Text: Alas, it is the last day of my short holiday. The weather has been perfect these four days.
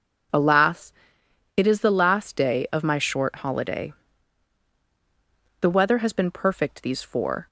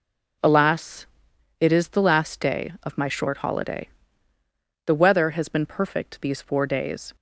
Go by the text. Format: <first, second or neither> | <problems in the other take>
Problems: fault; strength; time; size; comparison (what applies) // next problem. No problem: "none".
second | stops before "days"; at 7.4 s